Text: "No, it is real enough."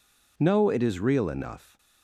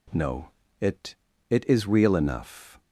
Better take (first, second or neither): first